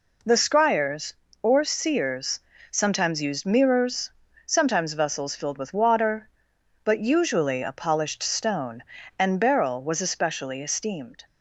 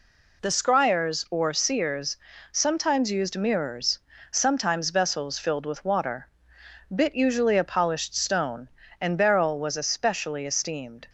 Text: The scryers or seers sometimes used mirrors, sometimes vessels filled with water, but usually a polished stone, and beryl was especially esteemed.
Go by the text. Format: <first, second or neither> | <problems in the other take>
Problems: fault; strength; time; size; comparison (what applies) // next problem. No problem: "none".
first | pauses between "seers" and "sometimes"; at 2.1 s; 0.38 s long; slight in the first // says "bit" for "but"; at 6.9 s